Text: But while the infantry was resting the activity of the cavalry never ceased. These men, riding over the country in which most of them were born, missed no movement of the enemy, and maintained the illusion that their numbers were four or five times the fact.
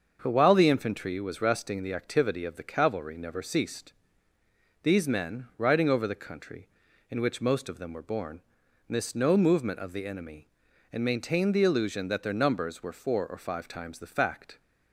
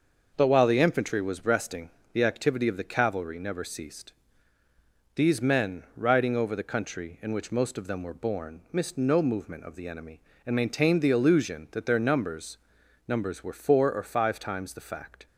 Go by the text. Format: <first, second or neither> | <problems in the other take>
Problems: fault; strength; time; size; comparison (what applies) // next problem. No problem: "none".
first | starts louder than the rest; until 1.3 s; 6 dB; also in the first // pauses between "resting" and "the"; slight; at 1.8 s; 0.22 s long // says "numbers" twice; at 13.0 s